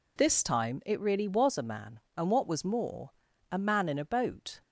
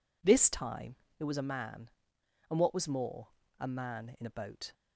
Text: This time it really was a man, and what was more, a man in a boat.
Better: first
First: none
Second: pauses between "time" and "it"; slight; at 0.9 s; 0.22 s long // skips "really"; at 1.2 s

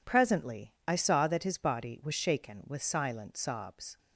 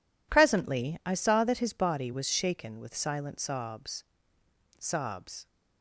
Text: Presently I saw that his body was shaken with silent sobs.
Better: first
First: none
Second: says "sobs" twice; at 4.7 s

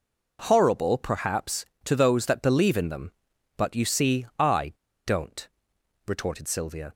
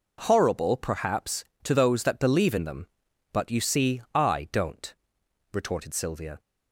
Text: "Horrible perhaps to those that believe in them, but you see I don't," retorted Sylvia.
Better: second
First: pauses between "I" and "don't"; slight; at 4.7 s; 0.33 s long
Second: none

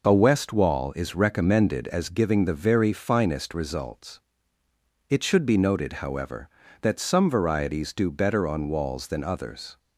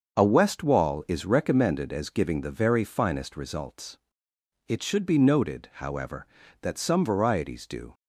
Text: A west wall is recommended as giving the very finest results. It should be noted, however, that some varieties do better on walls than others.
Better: first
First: none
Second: starts louder than the rest; until 1.1 s; 6.5 dB // stops before "better on walls than others"; at 7.9 s

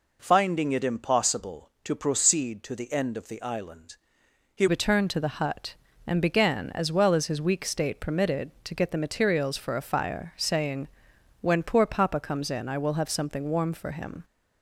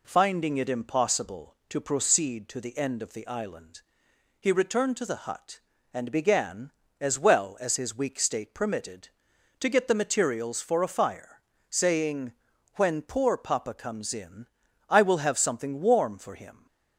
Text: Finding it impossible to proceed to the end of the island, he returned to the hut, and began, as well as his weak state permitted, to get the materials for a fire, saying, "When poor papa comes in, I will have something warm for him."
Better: second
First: changes voice at "returned"; from 4.6 s on; 9.6 s long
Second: none

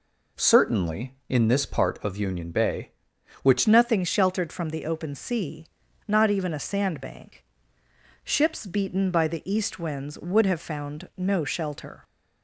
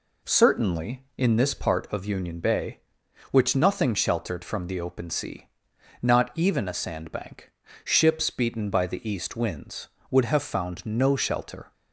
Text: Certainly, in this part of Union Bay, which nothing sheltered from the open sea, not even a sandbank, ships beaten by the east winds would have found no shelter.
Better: second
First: changes voice at "nothing"; from 3.6 s on; 8.4 s long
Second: none

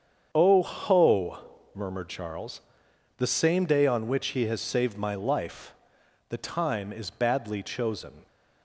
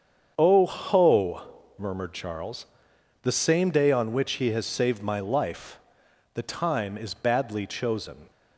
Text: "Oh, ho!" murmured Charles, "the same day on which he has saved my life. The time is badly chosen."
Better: neither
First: starts louder than the rest; strong; until 1.3 s; 7.5 dB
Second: starts louder than the rest; strong; until 1.3 s; 7.5 dB

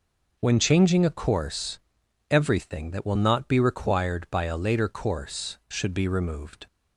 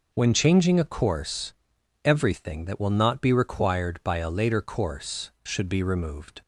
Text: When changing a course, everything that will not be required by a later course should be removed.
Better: neither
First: none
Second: none

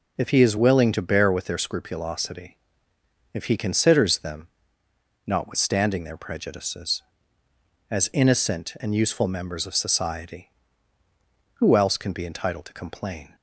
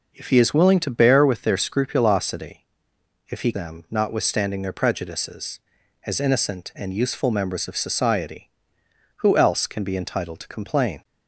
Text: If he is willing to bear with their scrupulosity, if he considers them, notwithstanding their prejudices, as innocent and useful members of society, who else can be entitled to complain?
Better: first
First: none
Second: skips "considers"; at 3.5 s

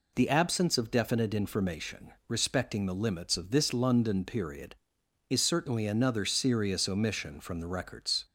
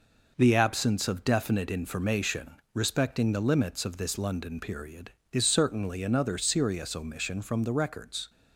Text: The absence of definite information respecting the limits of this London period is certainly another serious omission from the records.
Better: first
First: pauses between "information" and "respecting"; slight; at 2.1 s; 0.16 s long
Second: gets quieter; noticeable; throughout; 4.5 dB // pauses between "information" and "respecting"; slight; at 2.5 s; 0.18 s long

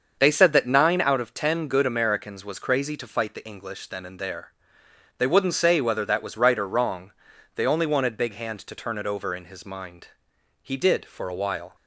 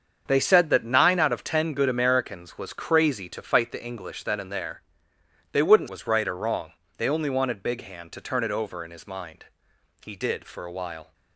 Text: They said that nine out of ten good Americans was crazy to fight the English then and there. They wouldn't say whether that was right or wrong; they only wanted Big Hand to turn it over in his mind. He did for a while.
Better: first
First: starts louder than the rest; until 1.2 s; 6.5 dB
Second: starts louder than the rest; strong; until 1.2 s; 7 dB // skips "say whether that"; at 5.8 s

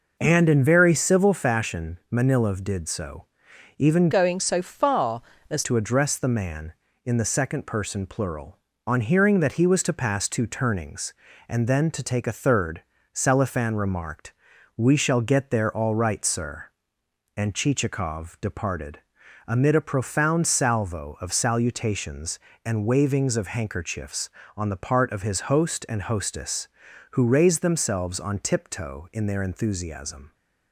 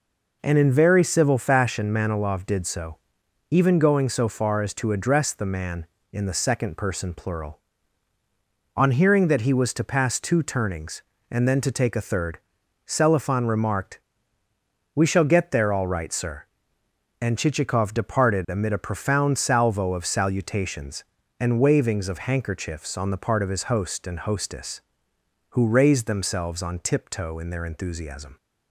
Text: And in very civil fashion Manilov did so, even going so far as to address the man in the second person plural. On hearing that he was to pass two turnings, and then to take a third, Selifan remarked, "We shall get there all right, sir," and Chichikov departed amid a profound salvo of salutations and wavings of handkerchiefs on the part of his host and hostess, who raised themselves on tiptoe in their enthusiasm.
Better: second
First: changes voice from "going" to "as"; from 4.1 to 5.6 s; 1.5 s long // pauses between "departed" and "amid"; noticeable; at 18.9 s; 0.50 s long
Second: none

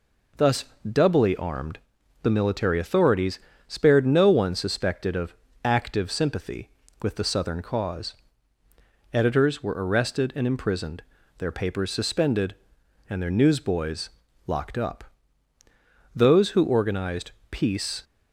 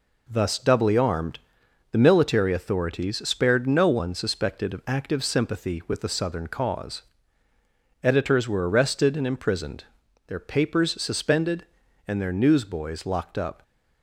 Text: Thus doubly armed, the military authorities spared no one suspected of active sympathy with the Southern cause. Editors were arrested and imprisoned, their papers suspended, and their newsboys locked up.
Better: second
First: pauses between "Thus" and "doubly"; slight; at 0.6 s; 0.24 s long // pauses between "authorities" and "spared"; slight; at 3.3 s; 0.28 s long // pauses between "of" and "active"; slight; at 5.3 s; 0.30 s long // pauses between "newsboys" and "locked"; at 14.0 s; 0.38 s long // goes on to say "Those who organized peace"; strong; from 16.1 s on; 1.8 s long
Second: none

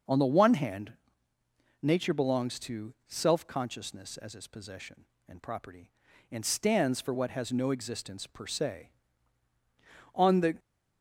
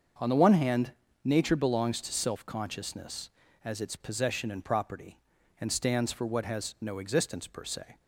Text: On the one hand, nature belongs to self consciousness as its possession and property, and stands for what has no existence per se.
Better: second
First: starts louder than the rest; noticeable; until 1.9 s; 6 dB // goes on to say "On the"; slight; from 10.1 s on; 0.42 s long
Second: starts louder than the rest; until 1.4 s; 6.5 dB

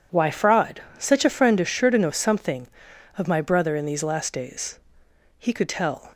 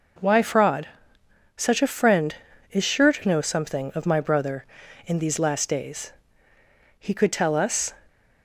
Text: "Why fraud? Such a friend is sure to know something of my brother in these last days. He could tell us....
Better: second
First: stops before "us"; at 6.1 s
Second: none

